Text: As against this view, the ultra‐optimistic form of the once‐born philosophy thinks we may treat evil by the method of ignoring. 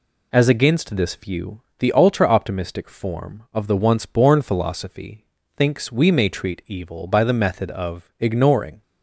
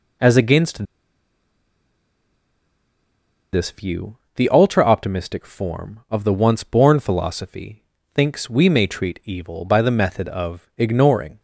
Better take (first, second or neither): first